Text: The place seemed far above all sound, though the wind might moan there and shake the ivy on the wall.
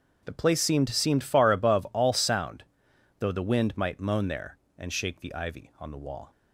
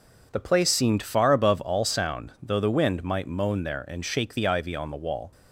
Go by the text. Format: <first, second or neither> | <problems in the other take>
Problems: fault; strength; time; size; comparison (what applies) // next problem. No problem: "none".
second | starts louder than the rest; until 1.2 s; 7 dB // says "seemed" twice; at 0.8 s